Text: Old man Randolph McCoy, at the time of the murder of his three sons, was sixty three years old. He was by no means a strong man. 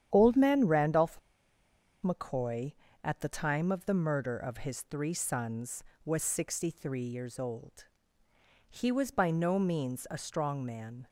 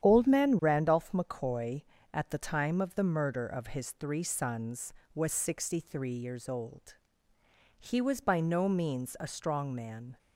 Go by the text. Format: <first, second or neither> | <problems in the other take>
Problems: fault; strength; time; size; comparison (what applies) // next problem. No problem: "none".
second | starts louder than the rest; strong; until 1.1 s; 9.5 dB; strong in the second // pauses between "Randolph" and "McCoy"; noticeable; at 1.1 s; 0.84 s long